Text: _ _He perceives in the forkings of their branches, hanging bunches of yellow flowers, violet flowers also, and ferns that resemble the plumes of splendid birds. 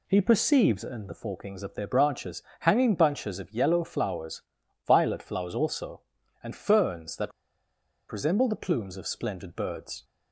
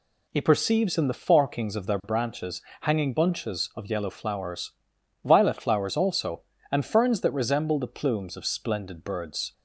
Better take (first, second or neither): second